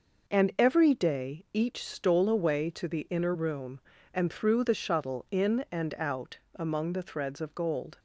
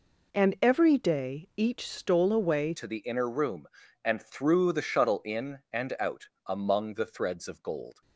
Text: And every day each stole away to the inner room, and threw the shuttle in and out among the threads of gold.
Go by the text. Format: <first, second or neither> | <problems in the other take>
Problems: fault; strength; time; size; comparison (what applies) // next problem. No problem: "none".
first | changes voice at "to"; from 2.7 s on; 5.3 s long // pauses between "out" and "among"; slight; at 6.2 s; 0.18 s long; slight in the first